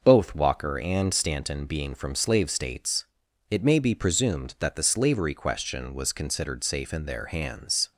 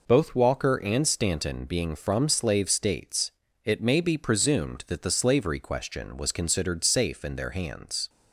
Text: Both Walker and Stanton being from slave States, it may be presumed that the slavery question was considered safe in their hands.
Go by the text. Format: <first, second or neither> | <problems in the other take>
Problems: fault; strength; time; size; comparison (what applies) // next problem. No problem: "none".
neither | none